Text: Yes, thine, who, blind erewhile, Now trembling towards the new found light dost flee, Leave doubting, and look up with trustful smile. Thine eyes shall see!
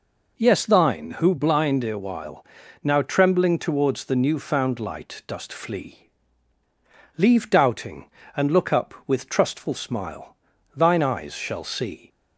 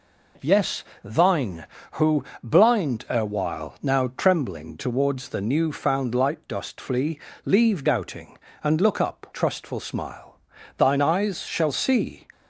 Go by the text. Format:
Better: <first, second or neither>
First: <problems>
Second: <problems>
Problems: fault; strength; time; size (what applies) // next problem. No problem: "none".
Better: first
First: none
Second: skips "with"; at 9.2 s